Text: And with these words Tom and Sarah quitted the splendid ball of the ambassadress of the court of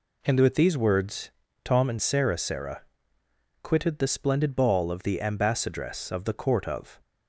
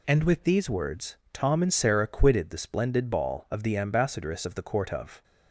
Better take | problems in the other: second | pauses between "words" and "Tom"; slight; at 1.3 s; 0.34 s long; slight in the second // says "Sarah" twice; at 2.3 s

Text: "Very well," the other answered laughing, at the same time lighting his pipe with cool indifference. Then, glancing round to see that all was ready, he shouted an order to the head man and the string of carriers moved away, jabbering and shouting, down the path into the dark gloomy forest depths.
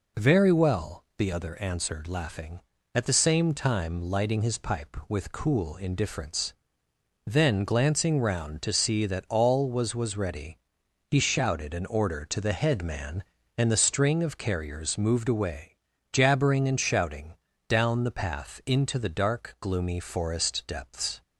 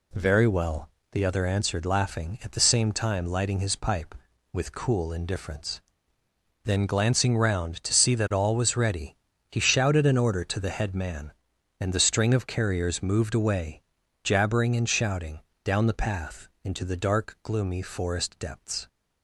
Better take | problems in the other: second | says "was" twice; at 9.9 s

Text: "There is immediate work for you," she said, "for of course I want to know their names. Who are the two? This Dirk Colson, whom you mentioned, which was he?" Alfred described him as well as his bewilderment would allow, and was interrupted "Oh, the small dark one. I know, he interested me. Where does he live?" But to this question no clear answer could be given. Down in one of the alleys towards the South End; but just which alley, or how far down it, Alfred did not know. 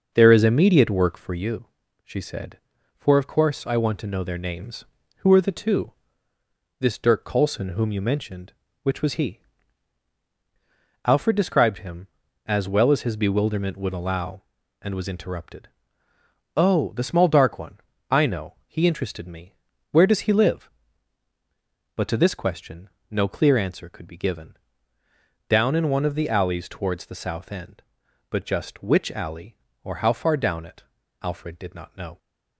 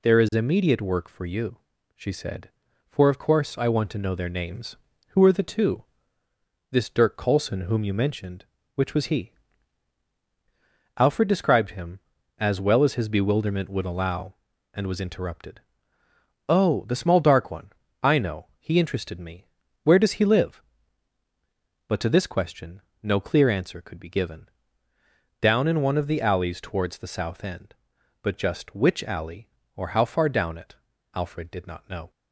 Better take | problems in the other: second | starts louder than the rest; noticeable; until 1.5 s; 6 dB // pauses between "interrupted" and "Oh"; noticeable; at 15.6 s; 0.88 s long; noticeable in the second // pauses between "question" and "no"; slight; at 22.8 s; 0.22 s long; slight in the second

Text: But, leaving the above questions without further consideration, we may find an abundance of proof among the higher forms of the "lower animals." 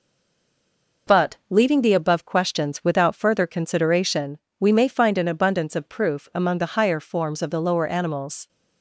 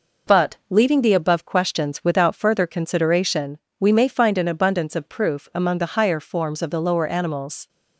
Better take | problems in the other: second | stays silent before the first word; until 1.0 s; 1.0 s long

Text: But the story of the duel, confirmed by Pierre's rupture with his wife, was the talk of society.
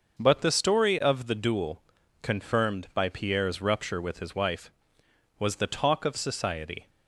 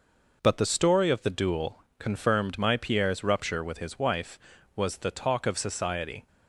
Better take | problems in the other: first | says "my" for "by"; at 2.5 s

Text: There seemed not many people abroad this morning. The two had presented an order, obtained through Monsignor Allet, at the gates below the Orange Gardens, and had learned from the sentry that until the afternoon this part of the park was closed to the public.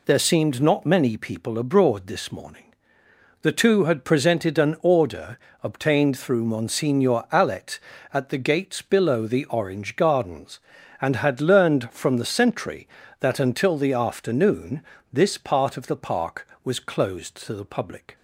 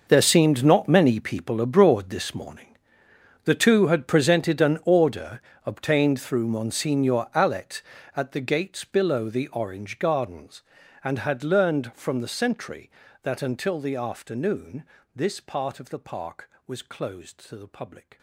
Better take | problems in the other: first | gets quieter; strong; throughout; 17 dB // pauses between "afternoon" and "this"; slight; at 14.8 s; 0.28 s long; slight in the first

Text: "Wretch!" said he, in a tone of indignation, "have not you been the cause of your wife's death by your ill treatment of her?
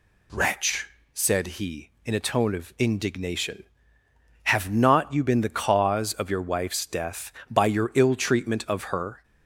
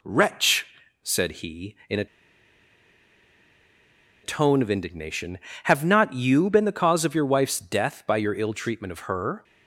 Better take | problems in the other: first | pauses between "a" and "tone"; strong; at 2.0 s; 2.1 s long

